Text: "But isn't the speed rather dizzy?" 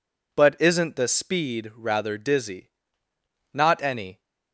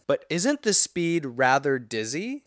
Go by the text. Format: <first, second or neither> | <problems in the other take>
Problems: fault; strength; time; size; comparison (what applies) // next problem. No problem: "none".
second | goes on to say "Not any"; noticeable; from 3.5 s on; 0.68 s long